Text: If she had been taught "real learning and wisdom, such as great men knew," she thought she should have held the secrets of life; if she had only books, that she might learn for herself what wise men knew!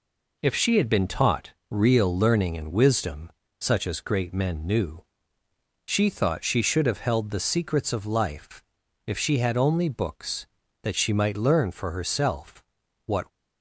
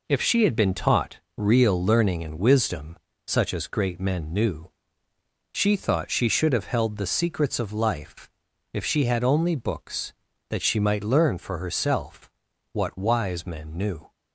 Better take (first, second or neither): second